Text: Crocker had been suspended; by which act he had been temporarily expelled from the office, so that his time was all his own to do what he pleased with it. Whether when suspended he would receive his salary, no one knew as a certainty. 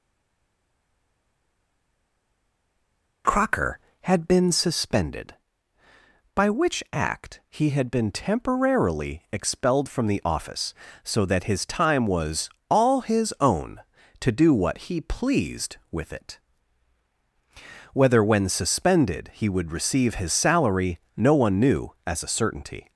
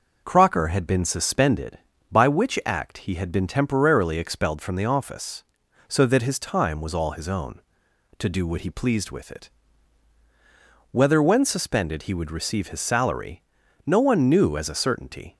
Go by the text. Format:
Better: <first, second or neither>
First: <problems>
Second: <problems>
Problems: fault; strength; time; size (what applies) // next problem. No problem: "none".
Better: second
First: stays silent before the first word; strong; until 3.2 s; 3.2 s long // pauses between "was" and "all"; slight; at 12.4 s; 0.22 s long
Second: none